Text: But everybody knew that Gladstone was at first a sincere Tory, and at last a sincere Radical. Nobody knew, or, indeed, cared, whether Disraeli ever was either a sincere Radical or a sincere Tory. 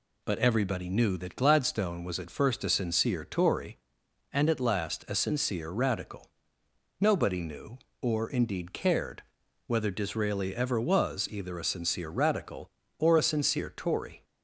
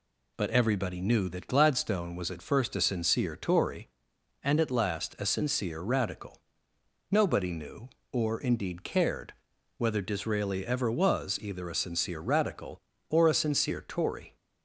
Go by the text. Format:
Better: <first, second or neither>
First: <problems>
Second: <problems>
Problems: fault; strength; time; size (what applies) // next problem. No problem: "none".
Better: neither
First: none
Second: none